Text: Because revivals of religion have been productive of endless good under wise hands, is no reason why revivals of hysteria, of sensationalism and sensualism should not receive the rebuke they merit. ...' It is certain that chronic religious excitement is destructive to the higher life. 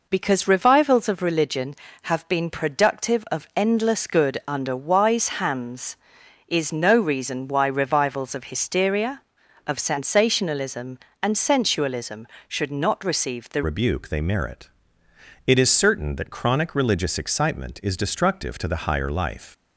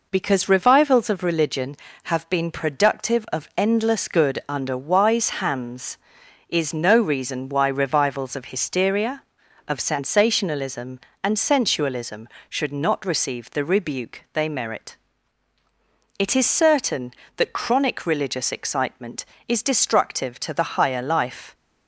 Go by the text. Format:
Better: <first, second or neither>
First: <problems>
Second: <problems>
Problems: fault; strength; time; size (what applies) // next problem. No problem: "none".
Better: second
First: changes voice at "rebuke"; from 13.6 s on; 5.9 s long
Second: none